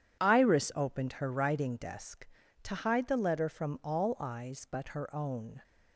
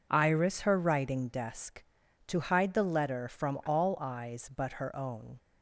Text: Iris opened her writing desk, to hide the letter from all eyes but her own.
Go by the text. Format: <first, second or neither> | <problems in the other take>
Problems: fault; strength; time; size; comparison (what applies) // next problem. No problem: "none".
first | skips "opened"; at 0.6 s